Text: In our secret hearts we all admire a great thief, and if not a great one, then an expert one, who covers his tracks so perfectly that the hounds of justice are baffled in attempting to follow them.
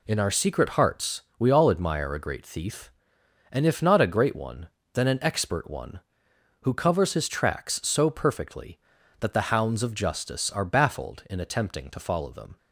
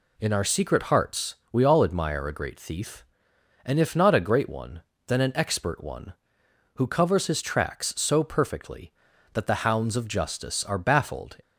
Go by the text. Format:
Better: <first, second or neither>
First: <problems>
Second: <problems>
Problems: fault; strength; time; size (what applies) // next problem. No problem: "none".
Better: first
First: pauses between "hearts" and "we"; slight; at 1.2 s; 0.18 s long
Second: pauses between "hearts" and "we"; slight; at 1.3 s; 0.18 s long // stops before "in attempting to follow them"; at 11.4 s